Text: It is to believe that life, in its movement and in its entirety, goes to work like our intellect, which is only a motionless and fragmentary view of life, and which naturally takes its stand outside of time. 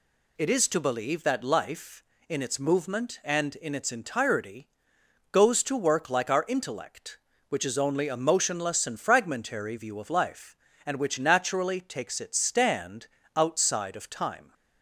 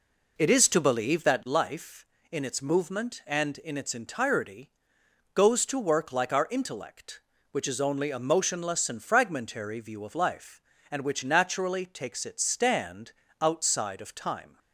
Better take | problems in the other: first | starts louder than the rest; noticeable; until 1.4 s; 4 dB // pauses between "stand" and "outside"; slight; at 13.1 s; 0.30 s long; slight in the first

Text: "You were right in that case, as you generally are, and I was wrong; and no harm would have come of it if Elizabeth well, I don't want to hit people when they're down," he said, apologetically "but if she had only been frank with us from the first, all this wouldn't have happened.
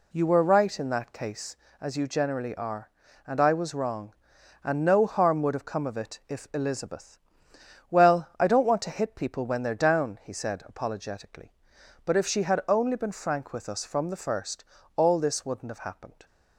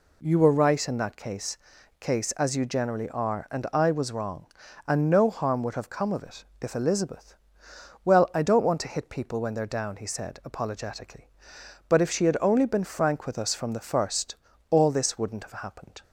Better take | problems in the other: first | says "case" twice; at 1.9 s // pauses between "it" and "if"; slight; at 6.4 s; 0.16 s long // pauses between "Elizabeth" and "well"; noticeable; at 7.3 s; 0.68 s long; noticeable in the first

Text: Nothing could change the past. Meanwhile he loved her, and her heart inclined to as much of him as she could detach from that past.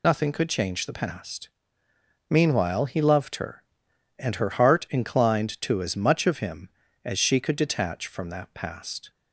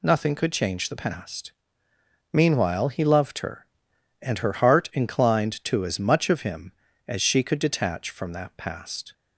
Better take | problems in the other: second | loses the start of "Nothing"; at 0.0 s; 50 ms

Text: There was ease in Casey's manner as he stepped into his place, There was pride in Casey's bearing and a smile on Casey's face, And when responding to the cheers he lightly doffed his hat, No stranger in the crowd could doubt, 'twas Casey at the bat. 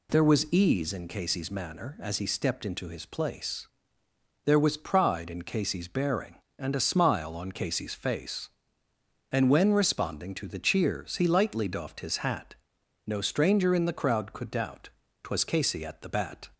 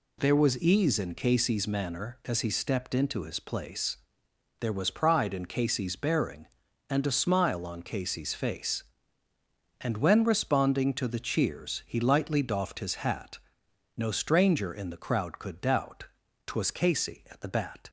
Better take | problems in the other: neither | none

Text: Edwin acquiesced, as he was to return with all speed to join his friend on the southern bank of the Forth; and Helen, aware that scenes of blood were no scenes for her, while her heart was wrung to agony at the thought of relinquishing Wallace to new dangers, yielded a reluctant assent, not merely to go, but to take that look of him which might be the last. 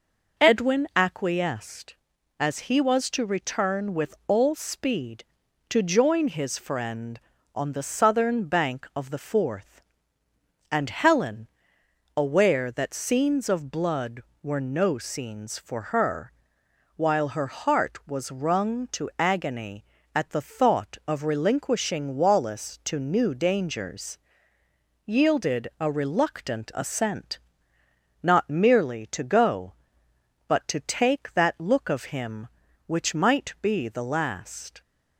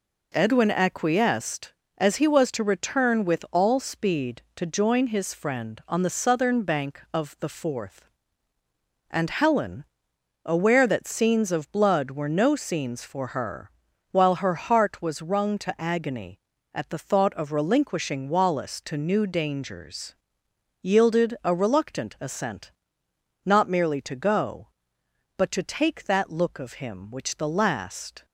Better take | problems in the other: first | skips "might be"; at 27.3 s

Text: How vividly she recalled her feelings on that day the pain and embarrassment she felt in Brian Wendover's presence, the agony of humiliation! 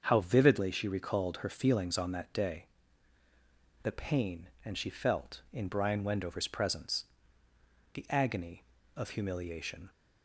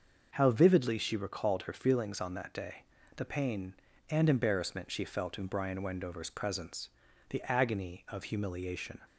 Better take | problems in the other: second | starts louder than the rest; until 1.0 s; 6.5 dB; noticeable in the second // pauses between "day" and "the"; at 2.6 s; 1.1 s long; slight in the second // skips "embarrassment"; at 4.7 s

